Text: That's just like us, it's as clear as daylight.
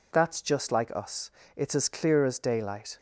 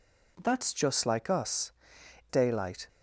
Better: first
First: none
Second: skips "it's as clear as"; at 2.0 s

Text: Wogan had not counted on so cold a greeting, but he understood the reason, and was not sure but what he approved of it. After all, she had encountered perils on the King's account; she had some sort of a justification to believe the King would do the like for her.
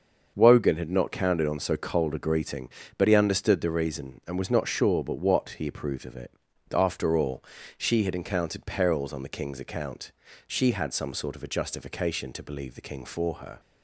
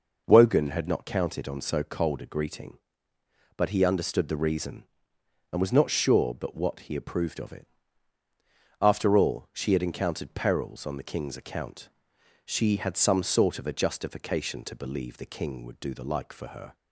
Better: second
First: starts louder than the rest; until 1.3 s; 6.5 dB // skips "would do the like"; at 13.0 s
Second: none

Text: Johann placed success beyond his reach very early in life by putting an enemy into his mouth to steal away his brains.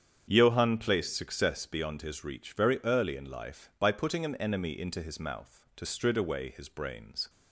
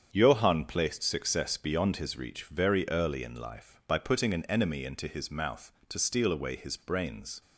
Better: second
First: starts louder than the rest; strong; until 1.3 s; 8 dB // says "strid" for "steal"; at 5.8 s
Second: starts louder than the rest; strong; until 1.1 s; 7.5 dB

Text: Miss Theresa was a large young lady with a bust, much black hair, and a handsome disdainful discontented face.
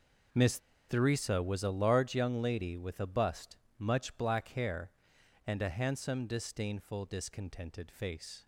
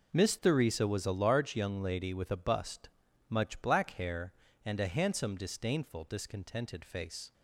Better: second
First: pauses between "Miss" and "Theresa"; slight; at 0.6 s; 0.28 s long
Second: none

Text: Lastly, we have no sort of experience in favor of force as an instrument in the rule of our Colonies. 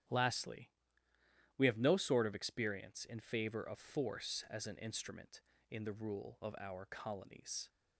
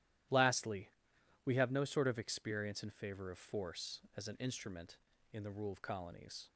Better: first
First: starts louder than the rest; strong; until 1.9 s; 11 dB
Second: starts louder than the rest; strong; until 1.8 s; 13 dB // skips "our"; at 5.8 s

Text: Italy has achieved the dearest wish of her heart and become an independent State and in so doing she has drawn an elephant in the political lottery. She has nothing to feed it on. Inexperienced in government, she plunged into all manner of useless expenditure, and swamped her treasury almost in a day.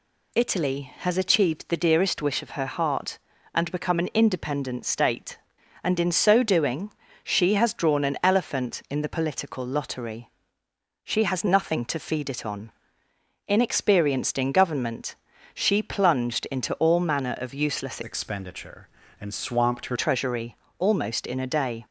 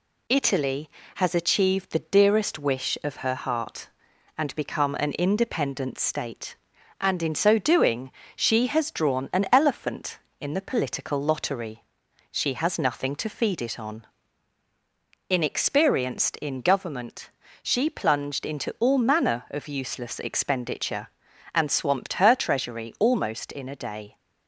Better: second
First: pauses between "doing" and "she"; slight; at 6.8 s; 0.32 s long // changes voice from "expenditure" to "her"; from 18.0 to 19.9 s; 1.9 s long // pauses between "treasury" and "almost"; slight; at 20.5 s; 0.24 s long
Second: pauses between "doing" and "she"; slight; at 8.0 s; 0.28 s long

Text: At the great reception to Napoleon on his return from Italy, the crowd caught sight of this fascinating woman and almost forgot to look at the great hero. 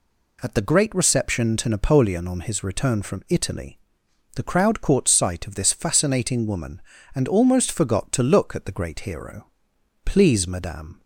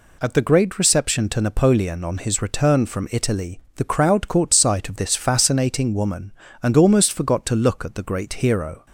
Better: second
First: goes on to say "Please Madame"; noticeable; from 10.0 s on; 0.96 s long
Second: none

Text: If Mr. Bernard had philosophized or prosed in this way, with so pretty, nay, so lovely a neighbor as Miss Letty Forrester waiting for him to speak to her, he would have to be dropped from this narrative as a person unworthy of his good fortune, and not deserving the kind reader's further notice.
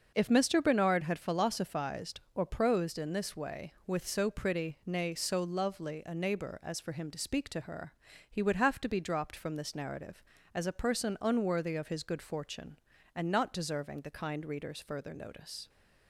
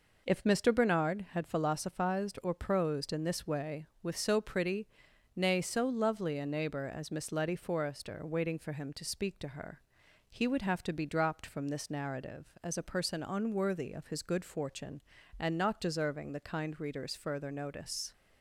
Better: second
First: starts louder than the rest; until 1.1 s; 6.5 dB // skips "Miss Letty Forrester waiting"; at 6.7 s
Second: none

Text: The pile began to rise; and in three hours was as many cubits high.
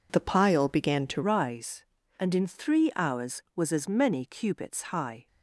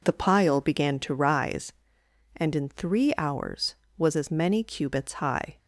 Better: second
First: changes voice at "rise"; from 1.2 s on; 4.0 s long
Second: none

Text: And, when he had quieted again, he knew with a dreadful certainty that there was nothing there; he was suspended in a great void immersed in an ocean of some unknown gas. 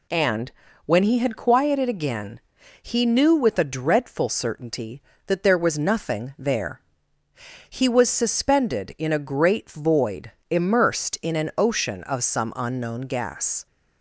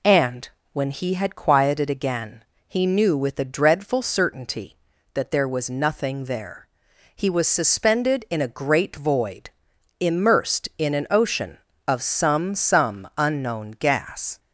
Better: first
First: pauses between "void" and "immersed"; slight; at 10.2 s; 0.18 s long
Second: pauses between "void" and "immersed"; noticeable; at 9.4 s; 0.50 s long // says "some" twice; at 12.5 s

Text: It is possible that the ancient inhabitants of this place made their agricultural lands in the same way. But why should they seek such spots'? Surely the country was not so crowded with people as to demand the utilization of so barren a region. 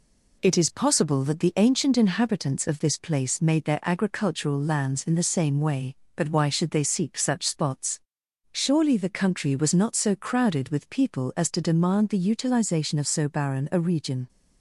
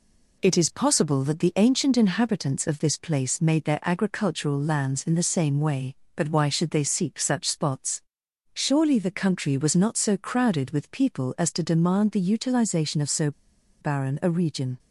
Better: first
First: none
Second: pauses between "so" and "barren"; noticeable; at 13.3 s; 0.50 s long

